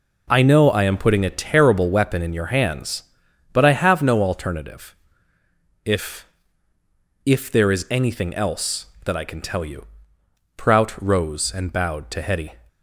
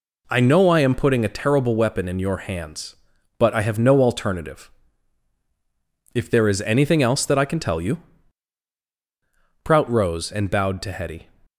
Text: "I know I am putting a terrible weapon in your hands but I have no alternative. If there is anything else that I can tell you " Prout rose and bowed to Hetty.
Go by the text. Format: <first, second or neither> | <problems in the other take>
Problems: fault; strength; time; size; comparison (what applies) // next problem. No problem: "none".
second | says "If" twice; at 7.2 s